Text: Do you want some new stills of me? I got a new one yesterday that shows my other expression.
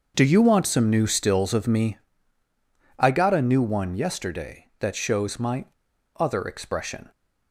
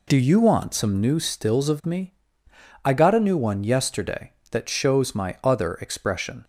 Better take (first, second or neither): second